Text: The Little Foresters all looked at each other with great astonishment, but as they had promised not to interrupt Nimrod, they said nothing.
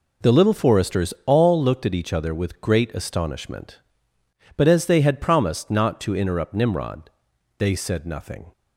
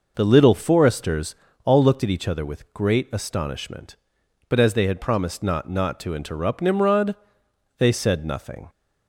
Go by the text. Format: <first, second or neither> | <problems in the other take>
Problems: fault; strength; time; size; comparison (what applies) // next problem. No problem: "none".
first | pauses between "Foresters" and "all"; slight; at 1.3 s; 0.30 s long // says "not" twice; at 5.6 s